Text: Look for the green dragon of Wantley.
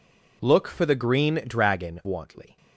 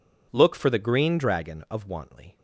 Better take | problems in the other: second | skips "of"; at 2.0 s

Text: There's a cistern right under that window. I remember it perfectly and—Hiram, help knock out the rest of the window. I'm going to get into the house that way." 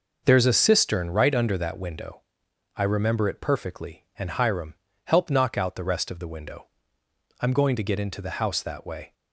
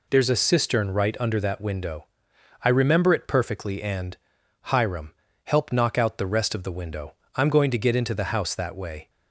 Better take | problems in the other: neither | none

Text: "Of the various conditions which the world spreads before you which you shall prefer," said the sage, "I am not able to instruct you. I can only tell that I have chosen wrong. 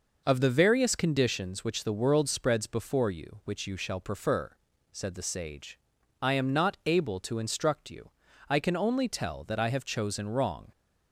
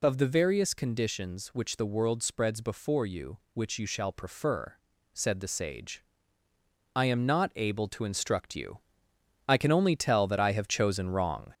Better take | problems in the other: first | gets louder; slight; throughout; 2.5 dB

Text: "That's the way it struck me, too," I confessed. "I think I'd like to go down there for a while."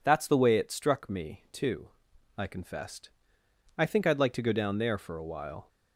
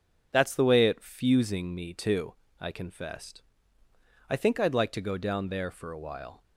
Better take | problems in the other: first | says "fusing" for "struck"; at 1.0 s

